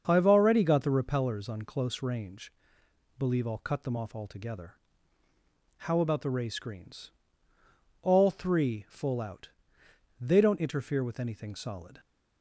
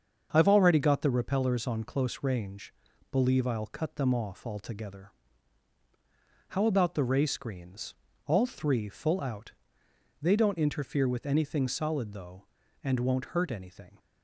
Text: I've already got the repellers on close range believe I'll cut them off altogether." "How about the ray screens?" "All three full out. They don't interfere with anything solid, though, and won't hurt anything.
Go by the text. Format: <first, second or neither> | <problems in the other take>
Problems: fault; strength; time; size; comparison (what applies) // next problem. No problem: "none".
second | starts louder than the rest; until 1.0 s; 7 dB; also in the second // pauses between "range" and "believe"; noticeable; at 2.5 s; 0.66 s long; also in the second // stops before "though and won't hurt anything"; at 11.9 s